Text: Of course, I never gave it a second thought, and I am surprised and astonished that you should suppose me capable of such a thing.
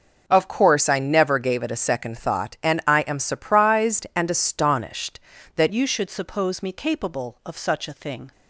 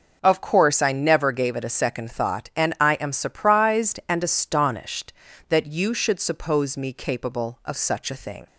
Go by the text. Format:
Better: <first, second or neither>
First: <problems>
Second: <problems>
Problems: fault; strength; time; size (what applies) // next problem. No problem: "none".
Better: second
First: changes voice at "you"; from 5.7 s on; 2.6 s long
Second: none